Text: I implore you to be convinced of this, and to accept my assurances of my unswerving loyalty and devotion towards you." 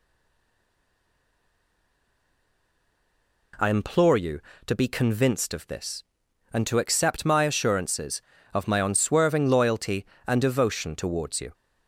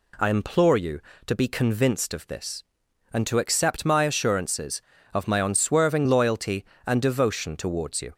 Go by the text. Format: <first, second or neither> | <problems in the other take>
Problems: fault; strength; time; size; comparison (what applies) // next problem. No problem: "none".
second | stays silent before the first word; strong; until 3.5 s; 3.5 s long